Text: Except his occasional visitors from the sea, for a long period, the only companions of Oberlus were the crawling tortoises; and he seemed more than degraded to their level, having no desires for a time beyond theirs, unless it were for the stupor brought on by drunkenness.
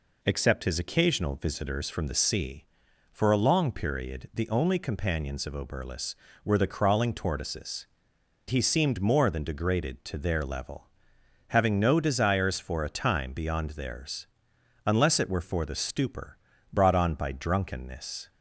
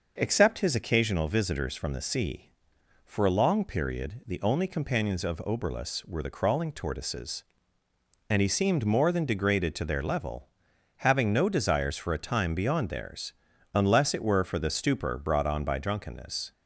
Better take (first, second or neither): second